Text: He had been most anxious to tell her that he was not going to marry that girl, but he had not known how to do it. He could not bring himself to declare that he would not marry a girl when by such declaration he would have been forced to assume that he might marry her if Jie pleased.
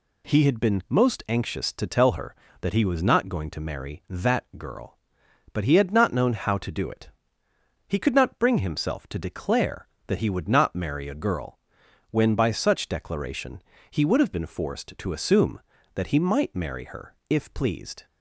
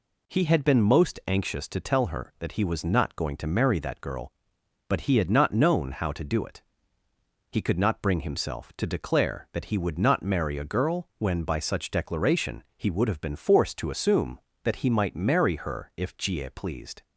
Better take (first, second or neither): second